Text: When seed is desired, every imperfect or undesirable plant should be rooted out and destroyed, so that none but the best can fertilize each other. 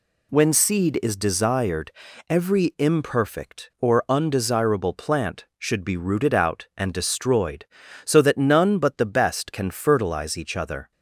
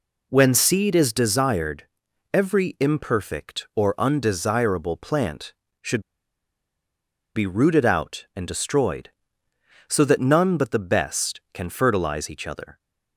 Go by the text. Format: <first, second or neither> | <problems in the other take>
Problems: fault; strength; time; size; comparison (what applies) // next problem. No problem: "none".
first | pauses between "should" and "be"; strong; at 6.0 s; 1.3 s long